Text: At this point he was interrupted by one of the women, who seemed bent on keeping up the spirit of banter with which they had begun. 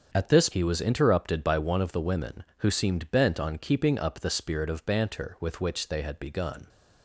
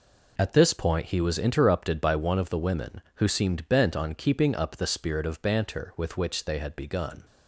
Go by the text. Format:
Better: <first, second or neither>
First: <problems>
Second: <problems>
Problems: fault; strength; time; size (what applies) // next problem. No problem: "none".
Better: second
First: starts louder than the rest; strong; until 1.1 s; 7 dB // skips "point"; at 0.5 s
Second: none